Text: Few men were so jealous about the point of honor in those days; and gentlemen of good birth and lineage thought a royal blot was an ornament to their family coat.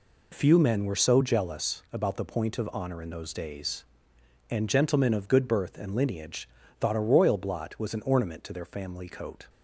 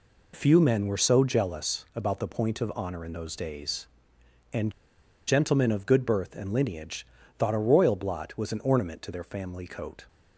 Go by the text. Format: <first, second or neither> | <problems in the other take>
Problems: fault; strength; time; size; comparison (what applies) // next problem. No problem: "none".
first | pauses between "and" and "gentlemen"; noticeable; at 4.7 s; 0.56 s long // pauses between "lineage" and "thought"; slight; at 7.0 s; 0.32 s long; slight in the first